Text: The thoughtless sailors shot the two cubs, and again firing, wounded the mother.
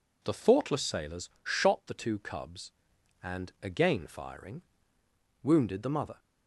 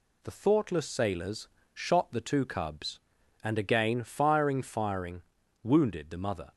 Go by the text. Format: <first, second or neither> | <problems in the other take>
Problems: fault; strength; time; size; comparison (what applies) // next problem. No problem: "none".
first | pauses between "sailors" and "shot"; slight; at 1.4 s; 0.24 s long; slight in the first // says "firing" twice; at 4.6 s